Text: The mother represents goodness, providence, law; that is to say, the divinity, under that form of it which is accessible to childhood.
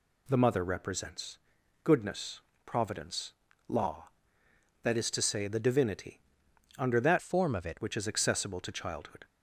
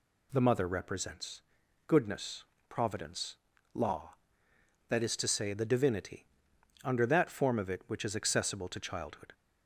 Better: second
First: pauses between "represents" and "goodness"; noticeable; at 1.3 s; 0.48 s long // changes voice from "form" to "it"; from 7.2 to 7.7 s; 0.5 s long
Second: pauses between "represents" and "goodness"; noticeable; at 1.4 s; 0.48 s long

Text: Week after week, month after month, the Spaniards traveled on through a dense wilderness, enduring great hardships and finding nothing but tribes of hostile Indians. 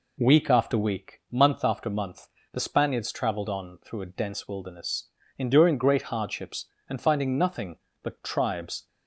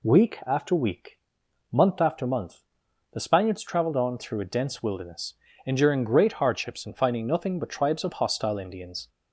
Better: second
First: stops before "of hostile Indians"; at 8.8 s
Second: none

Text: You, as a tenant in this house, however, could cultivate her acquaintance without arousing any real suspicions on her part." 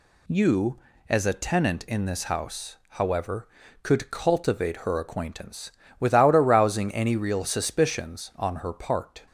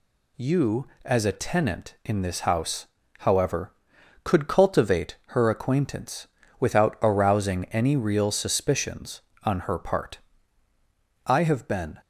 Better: first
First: pauses between "acquaintance" and "without"; slight; at 5.6 s; 0.30 s long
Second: pauses between "acquaintance" and "without"; slight; at 6.2 s; 0.32 s long // goes on to say "I have been"; noticeable; from 11.2 s on; 0.76 s long

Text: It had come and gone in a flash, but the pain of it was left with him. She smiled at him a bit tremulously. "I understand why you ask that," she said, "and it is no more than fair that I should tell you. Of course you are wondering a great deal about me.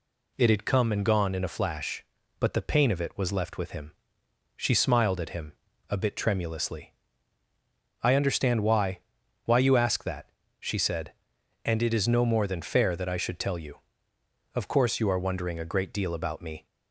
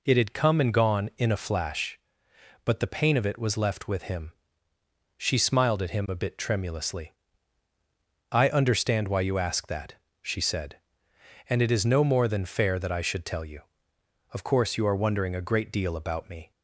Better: second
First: pauses between "him" and "a"; at 5.5 s; 0.40 s long // says "why" twice; at 9.4 s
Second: none

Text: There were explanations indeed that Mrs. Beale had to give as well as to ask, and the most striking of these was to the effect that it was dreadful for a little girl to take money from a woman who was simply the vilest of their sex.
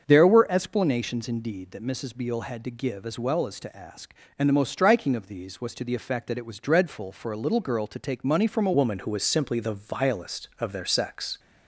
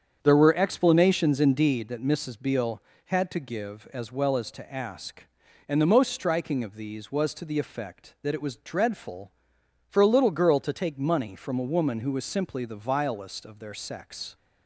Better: second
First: starts louder than the rest; until 1.1 s; 7 dB // changes voice at "woman"; from 8.7 s on; 2.6 s long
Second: starts louder than the rest; strong; until 1.2 s; 7.5 dB

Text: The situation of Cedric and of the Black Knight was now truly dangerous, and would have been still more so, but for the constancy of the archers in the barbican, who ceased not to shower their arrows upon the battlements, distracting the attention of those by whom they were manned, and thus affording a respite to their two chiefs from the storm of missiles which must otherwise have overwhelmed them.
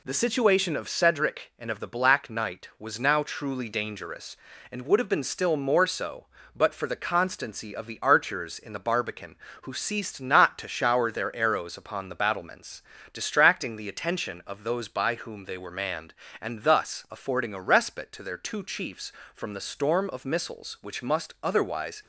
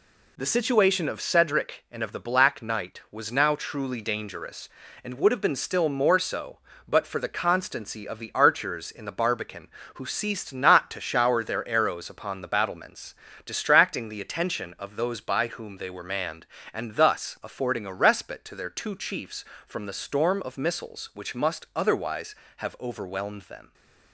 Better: second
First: stops before "have overwhelmed them"; at 22.0 s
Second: none

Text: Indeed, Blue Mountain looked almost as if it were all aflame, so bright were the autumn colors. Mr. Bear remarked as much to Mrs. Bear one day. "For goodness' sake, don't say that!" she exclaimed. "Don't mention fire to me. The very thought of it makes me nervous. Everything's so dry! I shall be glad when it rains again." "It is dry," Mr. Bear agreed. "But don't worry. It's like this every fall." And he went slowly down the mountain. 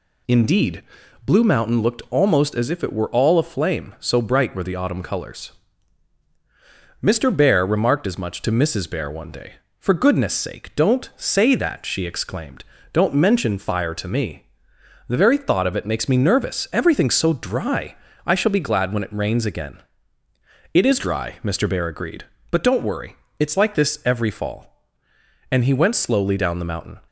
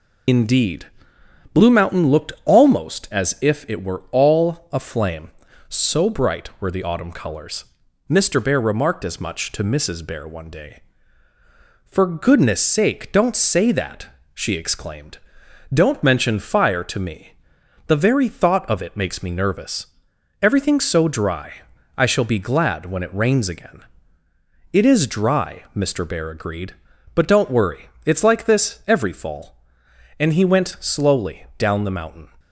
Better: first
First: none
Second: loses the start of "Indeed"; at 0.2 s; 65 ms

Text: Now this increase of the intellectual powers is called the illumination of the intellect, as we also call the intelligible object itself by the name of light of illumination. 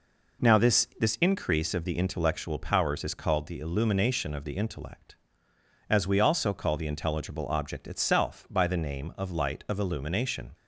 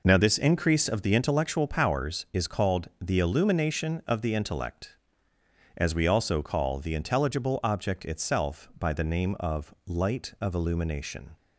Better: second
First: says "this" twice; at 0.9 s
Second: none

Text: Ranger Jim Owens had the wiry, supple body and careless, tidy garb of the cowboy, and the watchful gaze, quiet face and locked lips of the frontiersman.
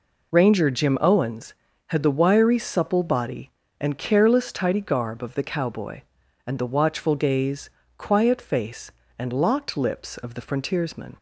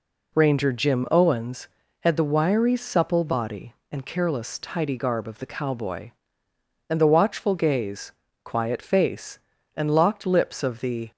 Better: first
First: none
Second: stops before "frontiersman"; at 11.1 s

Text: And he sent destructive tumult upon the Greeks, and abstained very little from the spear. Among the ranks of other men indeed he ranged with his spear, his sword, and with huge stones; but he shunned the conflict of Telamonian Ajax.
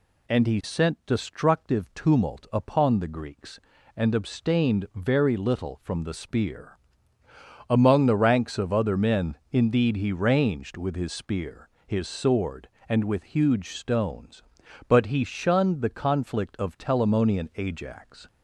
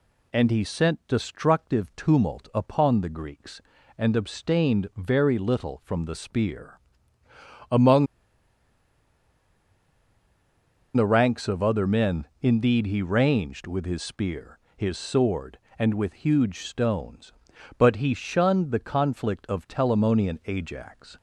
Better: first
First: none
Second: pauses between "Among" and "the"; strong; at 8.0 s; 2.8 s long

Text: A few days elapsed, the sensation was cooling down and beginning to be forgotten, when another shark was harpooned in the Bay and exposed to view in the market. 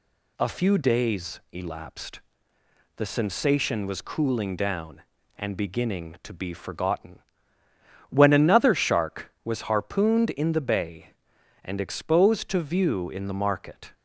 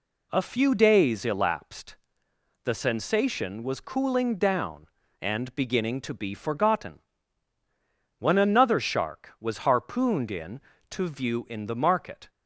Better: first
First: none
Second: skips "the Bay and exposed"; at 10.7 s

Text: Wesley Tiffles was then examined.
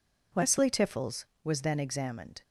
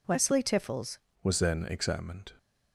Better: first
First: none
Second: changes voice at "was"; from 1.2 s on; 1.1 s long

